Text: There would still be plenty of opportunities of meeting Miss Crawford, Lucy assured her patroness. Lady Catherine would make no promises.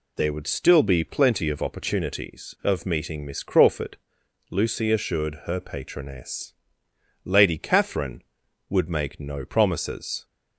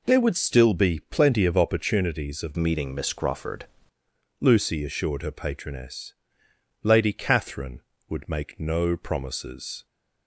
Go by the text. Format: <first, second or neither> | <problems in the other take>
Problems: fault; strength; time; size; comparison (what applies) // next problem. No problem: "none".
first | changes voice from "meeting" to "Crawford"; from 2.5 to 3.6 s; 1.1 s long